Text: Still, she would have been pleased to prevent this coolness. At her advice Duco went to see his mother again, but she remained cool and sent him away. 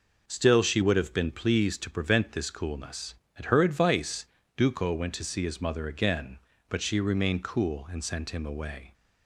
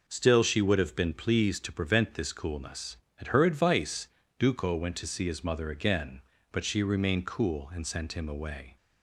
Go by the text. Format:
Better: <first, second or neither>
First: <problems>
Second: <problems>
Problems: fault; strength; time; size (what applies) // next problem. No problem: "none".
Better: neither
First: pauses between "advice" and "Duco"; slight; at 4.2 s; 0.30 s long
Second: pauses between "advice" and "Duco"; slight; at 4.0 s; 0.30 s long